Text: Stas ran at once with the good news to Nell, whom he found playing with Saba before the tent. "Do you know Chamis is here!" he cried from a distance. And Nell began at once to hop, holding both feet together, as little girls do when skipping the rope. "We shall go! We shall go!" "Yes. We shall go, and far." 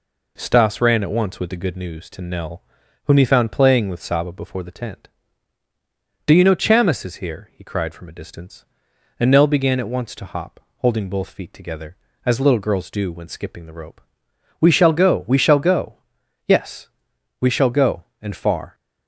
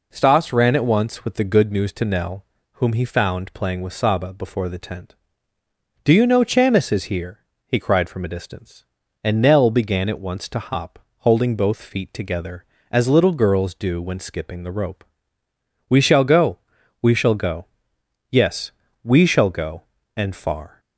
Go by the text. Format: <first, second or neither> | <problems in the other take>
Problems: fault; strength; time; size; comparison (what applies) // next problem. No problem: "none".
neither | none